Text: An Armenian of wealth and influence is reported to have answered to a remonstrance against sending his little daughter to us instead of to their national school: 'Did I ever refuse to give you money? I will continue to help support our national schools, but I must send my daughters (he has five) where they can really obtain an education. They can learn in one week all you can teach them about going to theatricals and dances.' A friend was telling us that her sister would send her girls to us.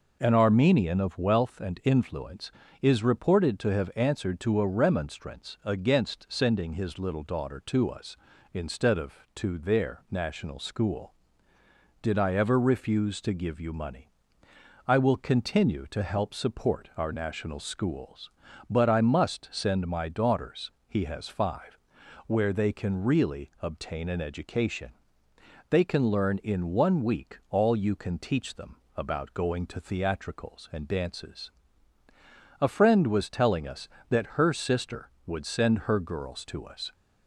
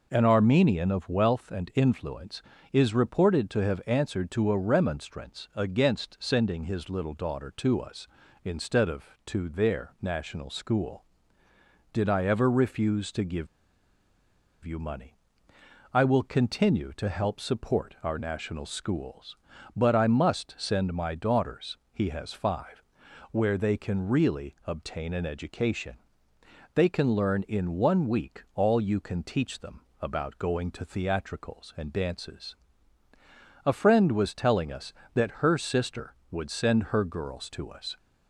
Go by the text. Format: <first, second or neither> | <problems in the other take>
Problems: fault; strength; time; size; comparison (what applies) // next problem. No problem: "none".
first | pauses between "give" and "you"; at 13.4 s; 1.1 s long // pauses between "them" and "about"; slight; at 29.8 s; 0.22 s long; slight in the first